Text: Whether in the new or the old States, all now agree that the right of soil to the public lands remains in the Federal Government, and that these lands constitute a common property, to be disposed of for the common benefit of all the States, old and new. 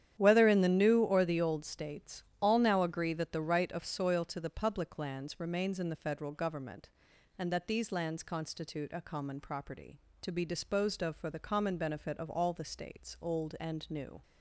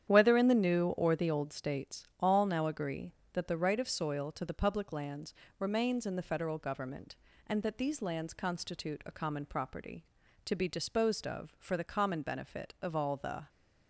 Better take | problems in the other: first | starts louder than the rest; strong; until 1.1 s; 9.5 dB; strong in the first // pauses between "lands" and "remains"; slight; at 5.3 s; 0.24 s long // stops before "States old and new"; at 13.4 s

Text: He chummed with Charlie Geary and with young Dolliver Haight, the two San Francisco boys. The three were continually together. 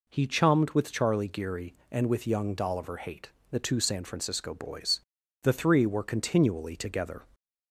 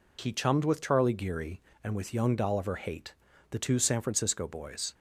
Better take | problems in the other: first | stops before "The three were continually together"; at 4.9 s

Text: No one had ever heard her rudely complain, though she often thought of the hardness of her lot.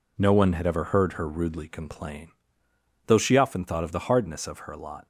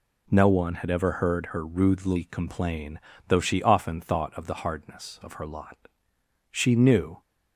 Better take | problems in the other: first | goes on to say "She knew"; noticeable; from 6.5 s on; 0.70 s long

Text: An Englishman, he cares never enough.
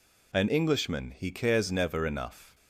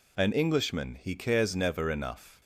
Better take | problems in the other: neither | none

